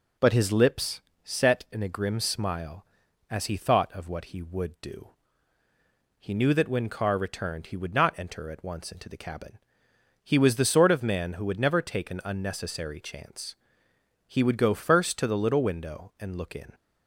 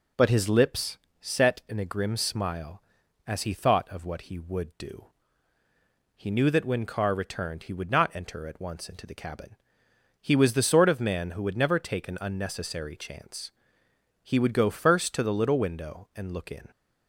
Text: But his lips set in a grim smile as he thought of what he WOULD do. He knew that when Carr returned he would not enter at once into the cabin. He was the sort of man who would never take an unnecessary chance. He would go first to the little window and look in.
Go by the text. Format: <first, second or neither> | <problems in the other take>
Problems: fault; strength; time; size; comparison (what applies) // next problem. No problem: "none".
neither | pauses between "lips" and "set"; slight; the same in both